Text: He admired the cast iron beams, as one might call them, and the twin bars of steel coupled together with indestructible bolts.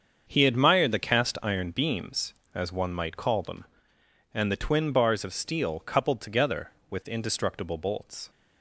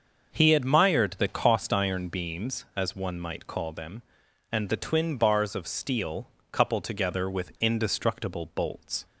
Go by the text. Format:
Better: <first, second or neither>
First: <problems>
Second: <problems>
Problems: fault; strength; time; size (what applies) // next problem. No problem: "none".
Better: first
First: starts louder than the rest; until 1.3 s; 7 dB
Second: starts louder than the rest; until 1.3 s; 6.5 dB // says "cost" for "cast"; at 1.2 s // pauses between "steel" and "coupled"; slight; at 6.2 s; 0.26 s long